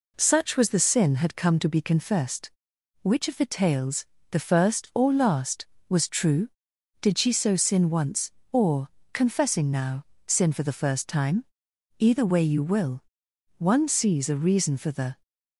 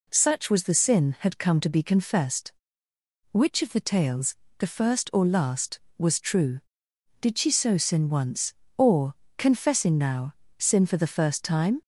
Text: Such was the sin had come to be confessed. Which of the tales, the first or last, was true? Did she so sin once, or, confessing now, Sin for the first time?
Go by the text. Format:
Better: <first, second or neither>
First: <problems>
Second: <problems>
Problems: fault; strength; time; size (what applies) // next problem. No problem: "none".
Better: second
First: goes on to say "Either way you will One sees a reason for the"; strong; from 11.9 s on; 3.2 s long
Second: none